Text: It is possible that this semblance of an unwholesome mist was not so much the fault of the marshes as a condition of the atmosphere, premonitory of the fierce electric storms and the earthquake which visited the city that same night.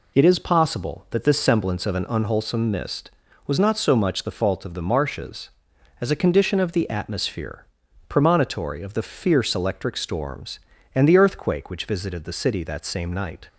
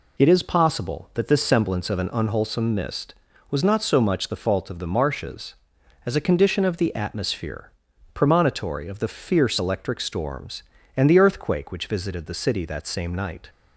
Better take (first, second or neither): neither